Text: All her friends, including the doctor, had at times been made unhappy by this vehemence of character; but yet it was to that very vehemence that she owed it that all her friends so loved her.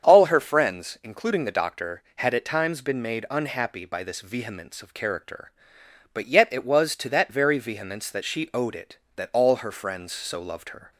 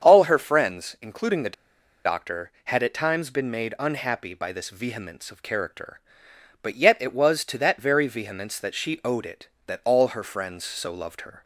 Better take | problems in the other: first | starts louder than the rest; strong; until 1.0 s; 7.5 dB; strong in the first // pauses between "the" and "doctor"; noticeable; at 1.5 s; 0.52 s long

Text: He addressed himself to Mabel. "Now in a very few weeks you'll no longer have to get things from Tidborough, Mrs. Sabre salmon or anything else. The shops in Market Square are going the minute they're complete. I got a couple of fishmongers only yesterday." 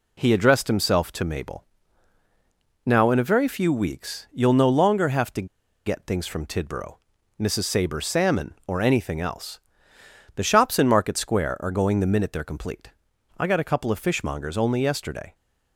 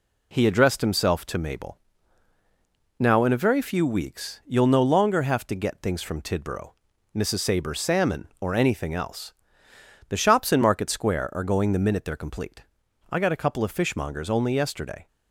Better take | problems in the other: second | pauses between "to" and "get"; at 5.4 s; 0.38 s long

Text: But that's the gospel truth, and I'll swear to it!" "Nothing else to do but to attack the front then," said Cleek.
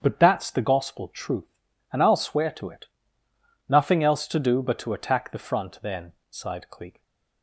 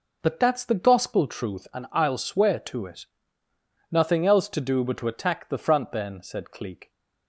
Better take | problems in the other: second | starts louder than the rest; strong; until 1.0 s; 8 dB // says "sighed" for "said"; at 6.3 s // stays silent after the last word; slight; from 6.9 s on; 0.5 s long

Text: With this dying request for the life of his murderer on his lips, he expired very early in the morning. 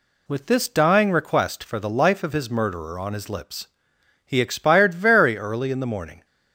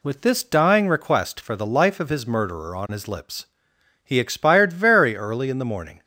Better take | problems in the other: neither | none

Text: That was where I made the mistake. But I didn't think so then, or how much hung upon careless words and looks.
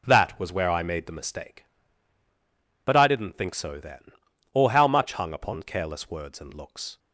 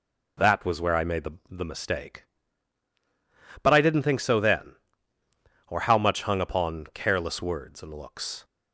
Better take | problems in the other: first | says "the" twice; at 1.5 s

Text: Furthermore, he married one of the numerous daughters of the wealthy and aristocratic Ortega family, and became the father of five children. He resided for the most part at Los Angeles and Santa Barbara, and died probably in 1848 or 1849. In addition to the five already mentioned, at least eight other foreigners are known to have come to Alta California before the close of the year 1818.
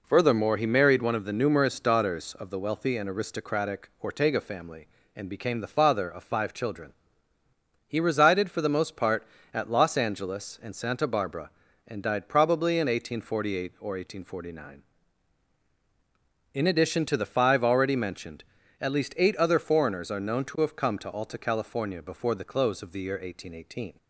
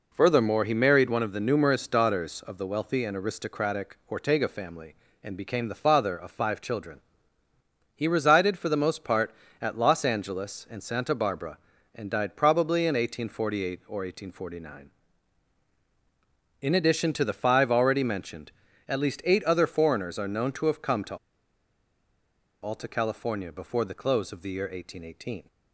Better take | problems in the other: first | pauses between "to" and "Alta"; strong; at 21.1 s; 1.4 s long

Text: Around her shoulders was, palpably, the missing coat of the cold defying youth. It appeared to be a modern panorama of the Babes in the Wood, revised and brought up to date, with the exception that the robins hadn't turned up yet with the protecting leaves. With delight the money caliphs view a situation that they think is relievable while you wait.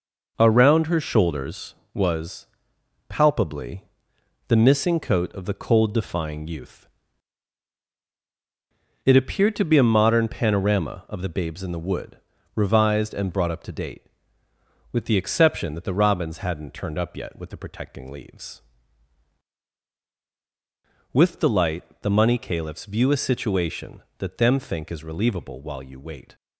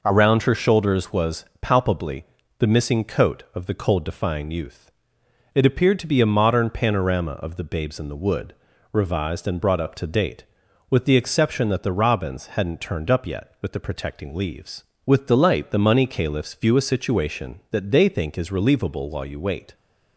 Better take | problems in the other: second | pauses between "delight" and "the"; slight; at 21.8 s; 0.16 s long // says "them" for "they"; at 24.3 s

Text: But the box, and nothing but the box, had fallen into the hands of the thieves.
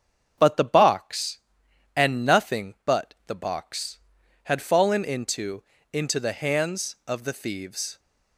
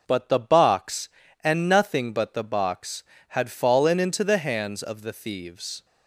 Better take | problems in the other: second | starts louder than the rest; strong; until 1.3 s; 7 dB // says "into" twice; at 5.9 s

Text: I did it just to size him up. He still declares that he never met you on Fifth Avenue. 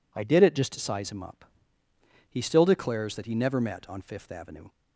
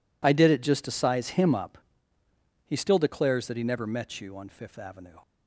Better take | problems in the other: second | skips "you"; at 3.8 s

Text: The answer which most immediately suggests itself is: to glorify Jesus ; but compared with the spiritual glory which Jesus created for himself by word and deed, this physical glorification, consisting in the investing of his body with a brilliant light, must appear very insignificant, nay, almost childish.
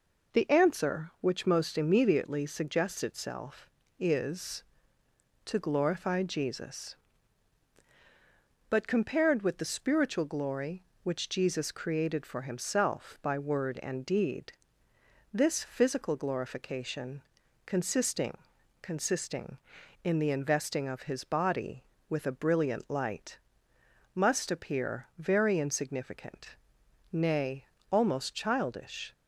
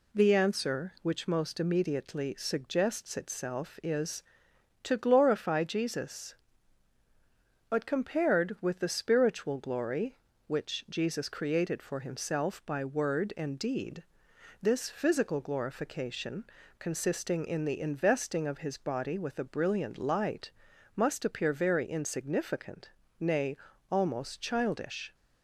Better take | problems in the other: second | says "consisting" twice; at 18.8 s

